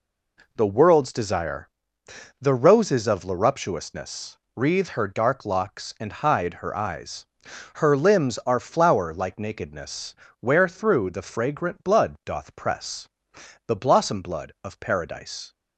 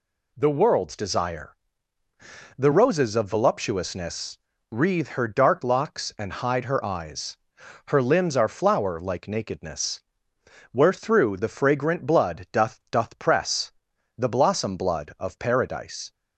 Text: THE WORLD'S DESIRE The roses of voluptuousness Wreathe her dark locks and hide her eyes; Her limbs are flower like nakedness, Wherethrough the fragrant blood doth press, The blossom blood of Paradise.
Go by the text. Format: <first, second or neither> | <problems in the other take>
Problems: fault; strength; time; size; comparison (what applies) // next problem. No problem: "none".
first | pauses between "DESIRE" and "The"; at 1.5 s; 1.0 s long; noticeable in the first // pauses between "voluptuousness" and "Wreathe"; slight; at 4.3 s; 0.34 s long; slight in the first // says "doth" twice; at 12.9 s